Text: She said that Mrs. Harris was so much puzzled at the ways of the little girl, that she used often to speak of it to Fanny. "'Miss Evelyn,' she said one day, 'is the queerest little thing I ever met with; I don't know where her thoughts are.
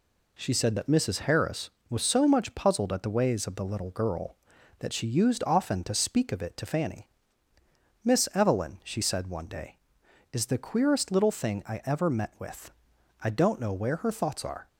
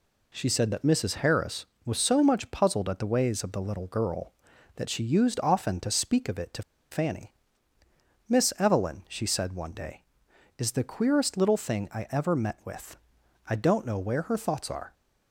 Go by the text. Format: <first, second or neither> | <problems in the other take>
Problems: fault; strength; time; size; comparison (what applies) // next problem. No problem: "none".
first | pauses between "to" and "Fanny"; slight; at 6.6 s; 0.28 s long